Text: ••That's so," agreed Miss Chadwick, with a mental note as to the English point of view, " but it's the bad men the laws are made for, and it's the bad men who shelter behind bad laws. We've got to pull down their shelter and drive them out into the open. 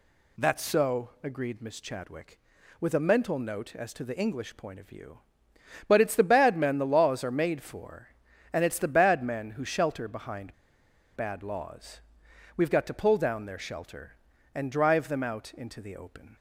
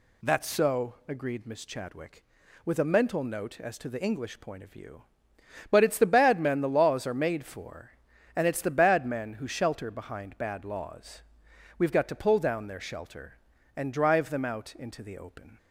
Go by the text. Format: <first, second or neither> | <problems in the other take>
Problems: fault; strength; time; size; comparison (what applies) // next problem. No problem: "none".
second | pauses between "behind" and "bad"; noticeable; at 10.5 s; 0.61 s long